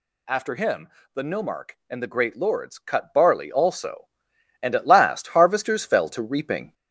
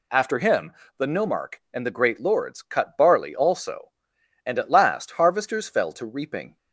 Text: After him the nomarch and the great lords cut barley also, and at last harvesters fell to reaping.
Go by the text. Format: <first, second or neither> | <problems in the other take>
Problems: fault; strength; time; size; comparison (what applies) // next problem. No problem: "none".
second | gets louder; throughout; 3.5 dB // pauses between "him" and "the"; slight; at 0.8 s; 0.24 s long; slight in the second